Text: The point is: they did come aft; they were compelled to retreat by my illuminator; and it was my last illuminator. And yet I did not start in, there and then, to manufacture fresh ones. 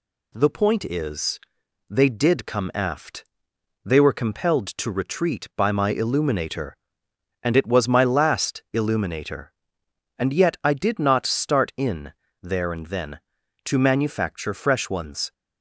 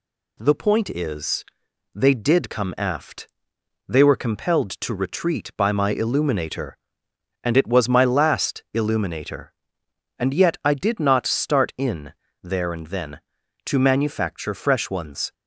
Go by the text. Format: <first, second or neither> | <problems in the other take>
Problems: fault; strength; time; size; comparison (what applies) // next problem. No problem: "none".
neither | none